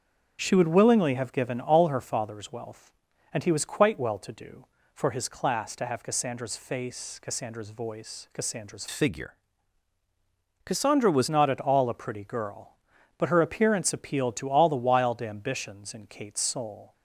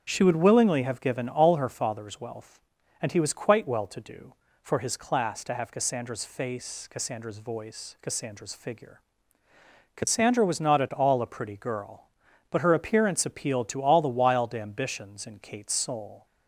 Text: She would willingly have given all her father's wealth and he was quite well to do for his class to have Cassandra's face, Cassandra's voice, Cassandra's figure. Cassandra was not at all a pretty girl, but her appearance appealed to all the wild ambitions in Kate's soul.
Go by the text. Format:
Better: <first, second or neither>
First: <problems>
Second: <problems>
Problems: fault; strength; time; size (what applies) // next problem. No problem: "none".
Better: second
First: starts louder than the rest; until 1.4 s; 6.5 dB // changes voice from "figure" to "was"; from 8.8 to 11.2 s; 2.4 s long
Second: starts louder than the rest; until 1.0 s; 6.5 dB